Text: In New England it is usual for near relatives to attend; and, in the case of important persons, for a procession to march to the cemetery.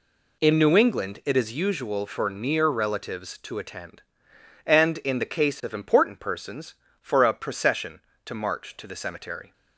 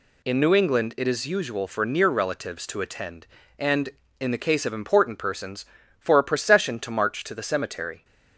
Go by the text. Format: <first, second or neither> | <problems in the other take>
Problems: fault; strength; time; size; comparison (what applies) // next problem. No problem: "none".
second | starts louder than the rest; slight; until 1.7 s; 2.5 dB